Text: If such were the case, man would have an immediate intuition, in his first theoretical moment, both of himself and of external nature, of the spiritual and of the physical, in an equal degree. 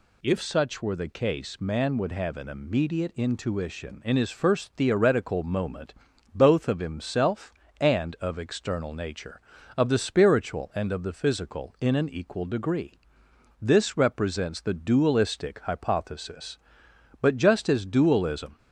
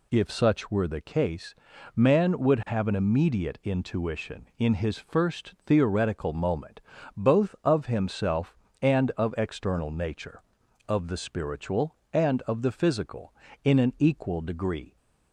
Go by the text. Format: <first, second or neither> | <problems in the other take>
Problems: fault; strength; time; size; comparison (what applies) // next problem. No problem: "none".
second | goes on to say "This represents the dualistic hypothesis But just as dualism"; strong; from 13.6 s on; 4.9 s long